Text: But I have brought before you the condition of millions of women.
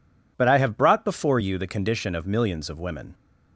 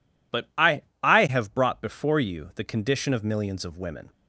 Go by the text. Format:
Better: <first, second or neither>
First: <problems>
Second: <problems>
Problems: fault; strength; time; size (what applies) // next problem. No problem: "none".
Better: first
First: none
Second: says "I" twice; at 1.0 s